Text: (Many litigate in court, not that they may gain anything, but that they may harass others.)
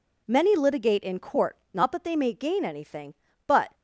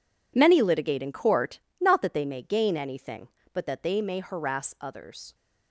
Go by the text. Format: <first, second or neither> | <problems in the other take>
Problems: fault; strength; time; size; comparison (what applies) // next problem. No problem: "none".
second | stops before "that they may harass others"; at 3.7 s